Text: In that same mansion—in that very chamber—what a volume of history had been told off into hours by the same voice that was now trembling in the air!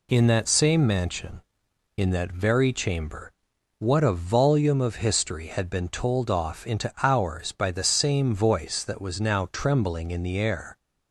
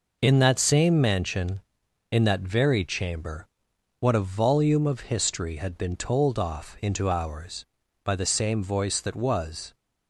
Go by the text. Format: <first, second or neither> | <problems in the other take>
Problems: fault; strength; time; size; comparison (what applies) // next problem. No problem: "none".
first | stops before "now trembling in the air"; at 9.7 s